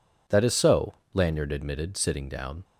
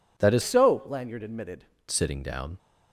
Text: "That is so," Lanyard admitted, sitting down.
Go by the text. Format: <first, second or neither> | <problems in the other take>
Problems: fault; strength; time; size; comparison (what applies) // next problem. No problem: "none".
first | changes voice from "so" to "admitted"; from 0.4 to 1.6 s; 1.2 s long